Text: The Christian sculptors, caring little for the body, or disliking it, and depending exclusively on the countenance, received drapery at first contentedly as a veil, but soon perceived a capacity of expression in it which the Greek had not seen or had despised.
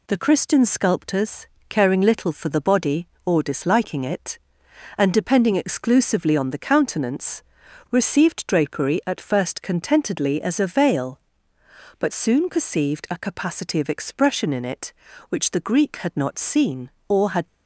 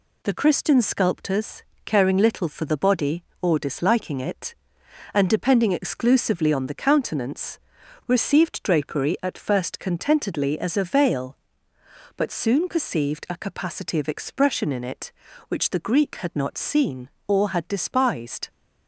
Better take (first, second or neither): second